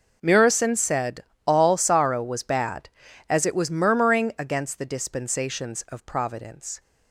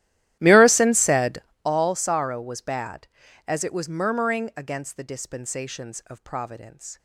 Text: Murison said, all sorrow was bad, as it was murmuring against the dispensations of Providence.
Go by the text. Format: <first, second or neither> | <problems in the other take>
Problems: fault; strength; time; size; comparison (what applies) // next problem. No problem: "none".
first | starts louder than the rest; strong; until 1.7 s; 13.5 dB